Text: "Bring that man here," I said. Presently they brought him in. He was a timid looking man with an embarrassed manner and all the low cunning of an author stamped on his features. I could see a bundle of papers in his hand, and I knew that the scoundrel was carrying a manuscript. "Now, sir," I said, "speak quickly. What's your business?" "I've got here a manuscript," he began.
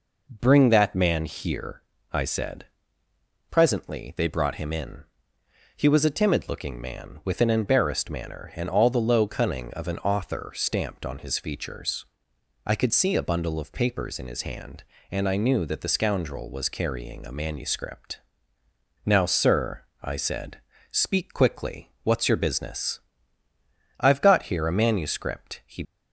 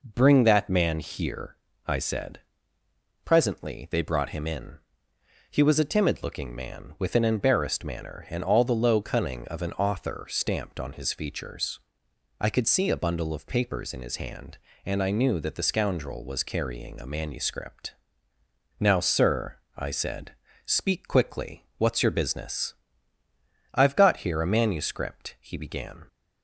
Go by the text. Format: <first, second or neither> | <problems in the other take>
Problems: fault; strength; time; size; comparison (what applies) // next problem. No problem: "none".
second | stops before "began"; at 25.8 s